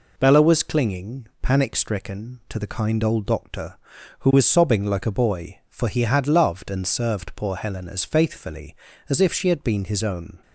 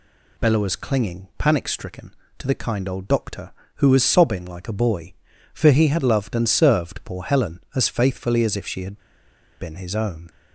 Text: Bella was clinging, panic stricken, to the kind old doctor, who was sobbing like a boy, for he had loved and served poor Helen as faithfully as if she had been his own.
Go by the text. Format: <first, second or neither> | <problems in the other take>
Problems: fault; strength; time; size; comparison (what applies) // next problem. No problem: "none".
first | pauses between "had" and "been"; noticeable; at 8.9 s; 0.64 s long